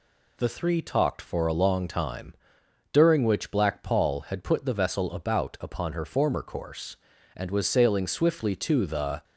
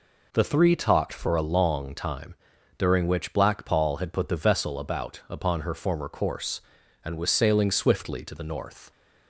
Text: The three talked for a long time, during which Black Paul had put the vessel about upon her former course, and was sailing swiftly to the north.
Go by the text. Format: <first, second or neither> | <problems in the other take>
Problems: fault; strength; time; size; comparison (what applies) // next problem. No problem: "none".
second | stops before "north"; at 9.2 s